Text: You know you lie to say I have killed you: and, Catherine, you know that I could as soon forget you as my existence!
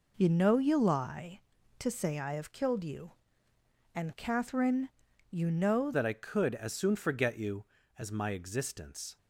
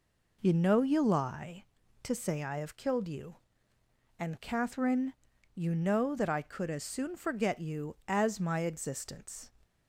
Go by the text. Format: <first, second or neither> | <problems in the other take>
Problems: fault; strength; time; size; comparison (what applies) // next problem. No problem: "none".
second | changes voice at "that"; from 5.9 s on; 3.2 s long